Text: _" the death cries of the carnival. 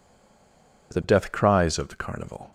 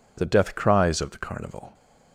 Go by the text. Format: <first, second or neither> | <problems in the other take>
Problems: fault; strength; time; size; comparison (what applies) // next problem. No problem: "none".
second | stays silent before the first word; slight; until 0.9 s; 0.9 s long